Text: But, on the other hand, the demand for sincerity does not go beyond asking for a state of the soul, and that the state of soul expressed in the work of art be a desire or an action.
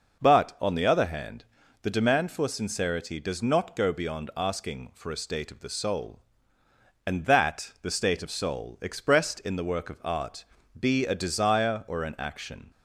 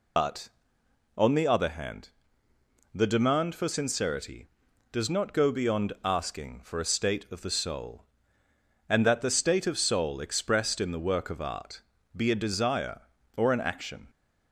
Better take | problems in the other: first | loses the start of "But"; at 0.1 s; 85 ms // pauses between "art" and "be"; slight; at 11.8 s; 0.34 s long; slight in the first

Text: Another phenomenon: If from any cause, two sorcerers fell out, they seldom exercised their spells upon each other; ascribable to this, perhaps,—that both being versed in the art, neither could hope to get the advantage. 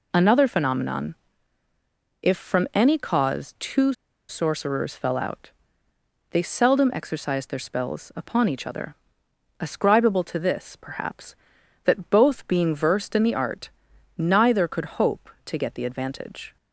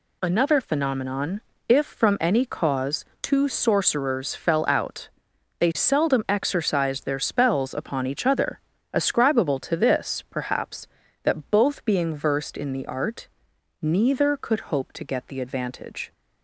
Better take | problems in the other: second | pauses between "two" and "sorcerers"; at 3.9 s; 0.36 s long

